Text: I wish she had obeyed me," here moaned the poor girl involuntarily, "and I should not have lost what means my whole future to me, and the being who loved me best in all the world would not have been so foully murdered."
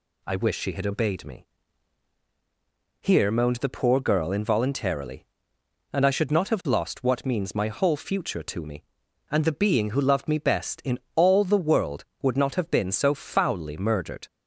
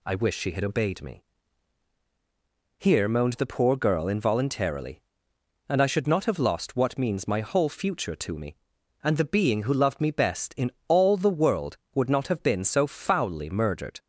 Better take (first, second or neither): neither